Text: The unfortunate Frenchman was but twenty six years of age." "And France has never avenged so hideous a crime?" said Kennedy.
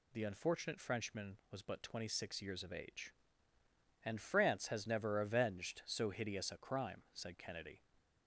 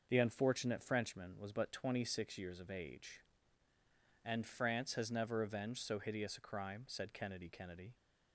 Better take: first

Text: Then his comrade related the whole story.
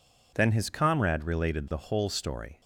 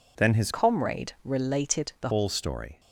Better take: first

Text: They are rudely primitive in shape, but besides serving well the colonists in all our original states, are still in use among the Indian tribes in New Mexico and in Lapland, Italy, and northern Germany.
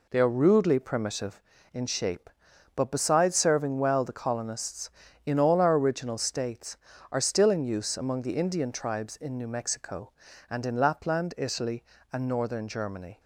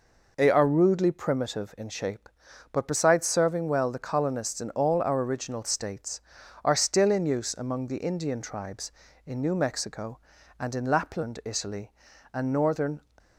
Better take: first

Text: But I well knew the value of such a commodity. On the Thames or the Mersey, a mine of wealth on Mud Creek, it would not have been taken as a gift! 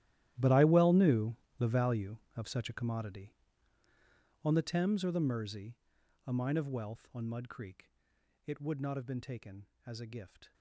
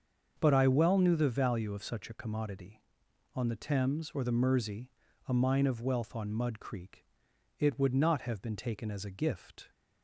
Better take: second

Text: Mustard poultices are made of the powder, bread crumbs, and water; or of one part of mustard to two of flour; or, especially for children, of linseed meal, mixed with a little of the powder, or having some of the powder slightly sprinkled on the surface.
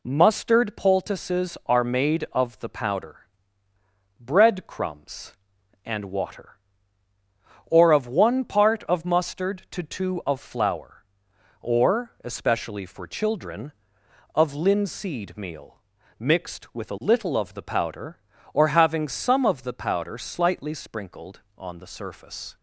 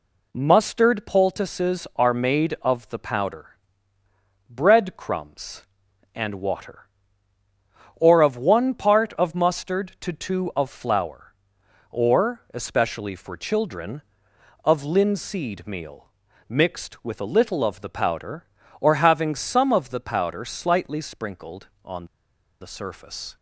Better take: first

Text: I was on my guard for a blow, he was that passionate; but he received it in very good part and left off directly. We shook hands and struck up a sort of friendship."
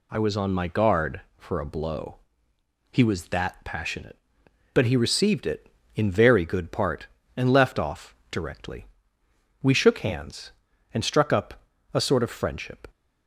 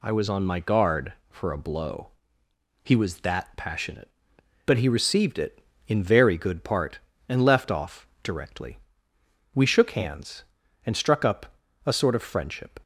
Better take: neither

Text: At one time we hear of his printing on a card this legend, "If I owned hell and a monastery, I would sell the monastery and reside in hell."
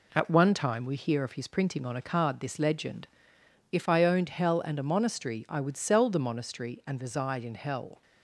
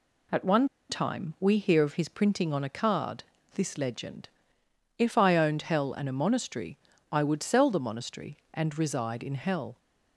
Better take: first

